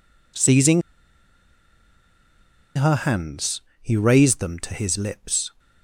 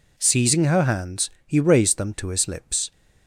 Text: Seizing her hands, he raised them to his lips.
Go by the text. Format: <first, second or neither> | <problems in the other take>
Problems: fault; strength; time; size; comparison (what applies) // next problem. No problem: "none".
second | pauses between "Seizing" and "her"; strong; at 0.8 s; 1.9 s long